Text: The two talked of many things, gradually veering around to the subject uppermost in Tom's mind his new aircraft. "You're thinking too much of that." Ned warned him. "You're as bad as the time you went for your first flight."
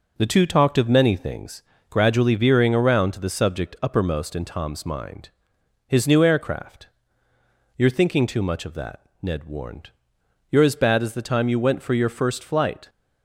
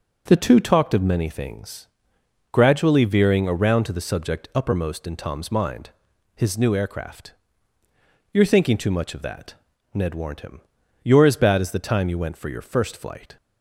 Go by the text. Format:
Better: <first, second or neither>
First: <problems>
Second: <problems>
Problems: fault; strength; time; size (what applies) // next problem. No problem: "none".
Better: second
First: pauses between "mind" and "his"; noticeable; at 5.2 s; 0.60 s long // skips "him"; at 10.2 s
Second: pauses between "mind" and "his"; at 5.9 s; 0.44 s long